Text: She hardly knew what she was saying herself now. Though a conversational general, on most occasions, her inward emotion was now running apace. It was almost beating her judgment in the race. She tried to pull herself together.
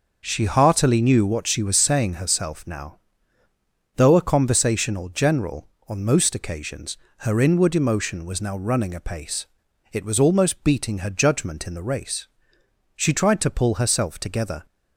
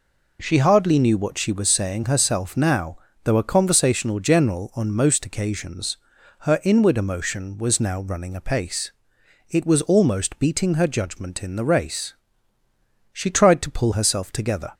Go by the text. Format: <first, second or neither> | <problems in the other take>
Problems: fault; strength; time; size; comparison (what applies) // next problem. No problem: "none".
second | says "heartily" for "hardly"; at 0.4 s